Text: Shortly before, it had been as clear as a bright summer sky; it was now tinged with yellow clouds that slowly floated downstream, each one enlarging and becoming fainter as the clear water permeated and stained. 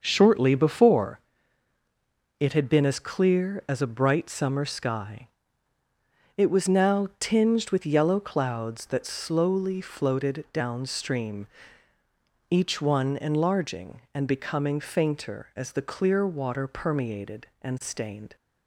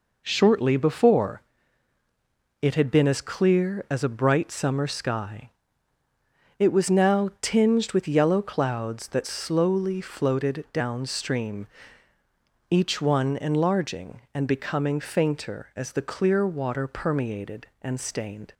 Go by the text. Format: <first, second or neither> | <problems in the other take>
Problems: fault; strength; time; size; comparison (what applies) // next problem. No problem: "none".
second | starts louder than the rest; until 1.1 s; 6.5 dB